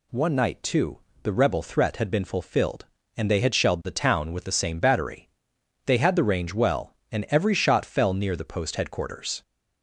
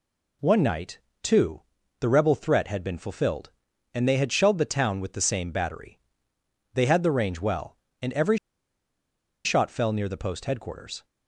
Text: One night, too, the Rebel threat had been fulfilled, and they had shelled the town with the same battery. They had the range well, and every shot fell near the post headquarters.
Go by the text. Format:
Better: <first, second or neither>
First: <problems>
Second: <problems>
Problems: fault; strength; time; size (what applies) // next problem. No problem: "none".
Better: first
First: none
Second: pauses between "every" and "shot"; at 8.3 s; 1.0 s long